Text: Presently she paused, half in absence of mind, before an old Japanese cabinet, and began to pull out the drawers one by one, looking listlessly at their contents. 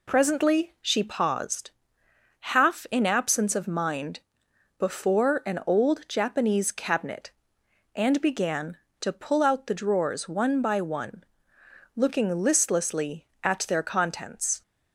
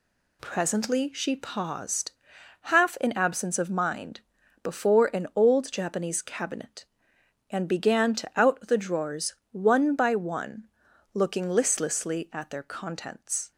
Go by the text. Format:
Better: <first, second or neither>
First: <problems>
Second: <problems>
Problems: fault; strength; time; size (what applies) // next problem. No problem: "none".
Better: first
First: none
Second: skips "pull"; at 8.3 s // pauses between "drawers" and "one"; slight; at 9.3 s; 0.18 s long